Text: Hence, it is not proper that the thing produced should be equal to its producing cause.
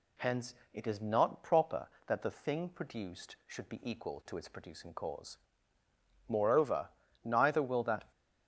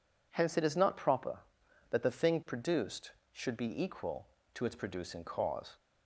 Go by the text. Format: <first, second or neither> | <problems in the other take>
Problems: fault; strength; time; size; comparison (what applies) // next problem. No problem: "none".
second | goes on to say "Moreover neither will that"; strong; from 6.2 s on; 1.8 s long